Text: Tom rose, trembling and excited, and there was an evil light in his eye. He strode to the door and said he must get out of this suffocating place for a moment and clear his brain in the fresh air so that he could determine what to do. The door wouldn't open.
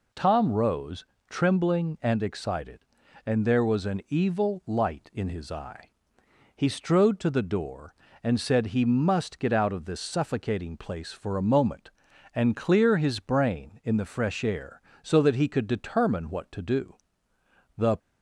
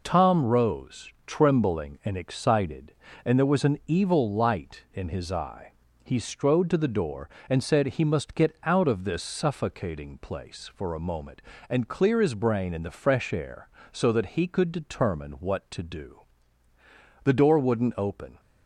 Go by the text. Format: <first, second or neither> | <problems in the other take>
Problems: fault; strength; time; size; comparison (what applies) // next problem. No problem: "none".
second | stops before "door wouldn't open"; at 17.9 s